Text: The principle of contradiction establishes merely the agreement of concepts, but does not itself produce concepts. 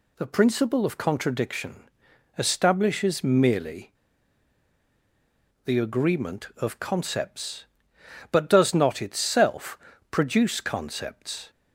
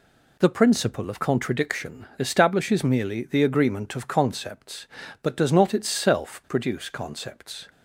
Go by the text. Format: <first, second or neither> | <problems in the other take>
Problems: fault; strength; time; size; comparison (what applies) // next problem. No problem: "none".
second | pauses between "contradiction" and "establishes"; noticeable; at 1.8 s; 0.48 s long // pauses between "merely" and "the"; strong; at 3.9 s; 1.7 s long // pauses between "itself" and "produce"; slight; at 9.7 s; 0.32 s long